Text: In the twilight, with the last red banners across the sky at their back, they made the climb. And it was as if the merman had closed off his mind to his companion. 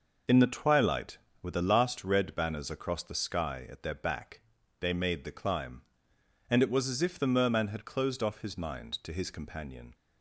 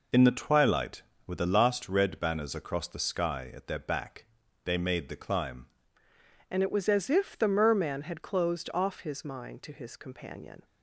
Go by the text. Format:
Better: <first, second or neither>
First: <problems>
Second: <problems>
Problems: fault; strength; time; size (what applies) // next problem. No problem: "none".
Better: first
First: none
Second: changes voice at "And"; from 6.4 s on; 4.2 s long